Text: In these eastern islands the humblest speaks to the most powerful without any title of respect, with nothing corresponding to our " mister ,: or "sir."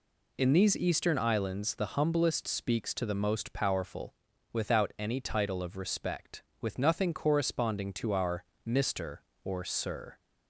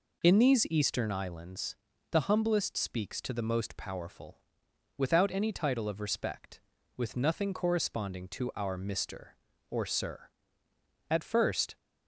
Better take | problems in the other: first | pauses between "islands" and "the"; slight; at 1.7 s; 0.34 s long // pauses between "powerful" and "without"; noticeable; at 4.4 s; 0.56 s long; also in the first // goes on to say "At first"; noticeable; from 11.0 s on; 0.68 s long

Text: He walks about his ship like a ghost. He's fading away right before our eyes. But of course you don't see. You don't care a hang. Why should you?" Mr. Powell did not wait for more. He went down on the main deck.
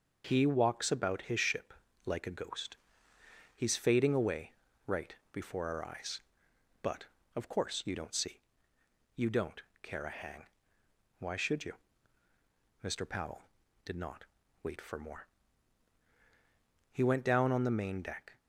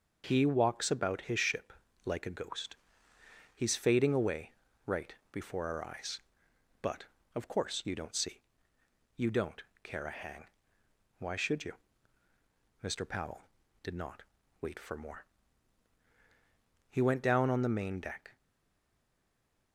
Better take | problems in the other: first | pauses between "ship" and "like"; slight; at 1.7 s; 0.32 s long; slight in the first // pauses between "away" and "right"; slight; at 4.5 s; 0.34 s long; slight in the first // pauses between "right" and "before"; slight; at 5.1 s; 0.18 s long; slight in the first // pauses between "don't" and "care"; slight; at 9.6 s; 0.22 s long; slight in the first // pauses between "not" and "wait"; at 14.2 s; 0.38 s long; also in the first // stays silent after the last word; noticeable; from 18.3 s on; 1.4 s long

